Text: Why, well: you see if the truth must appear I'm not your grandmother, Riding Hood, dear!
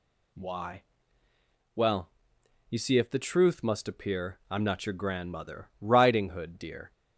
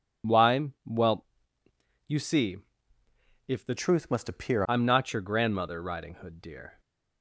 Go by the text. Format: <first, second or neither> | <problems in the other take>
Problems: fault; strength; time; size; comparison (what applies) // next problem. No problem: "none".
first | pauses between "see" and "if"; noticeable; at 2.5 s; 0.92 s long // changes voice from "truth" to "appear"; from 3.7 to 4.6 s; 0.9 s long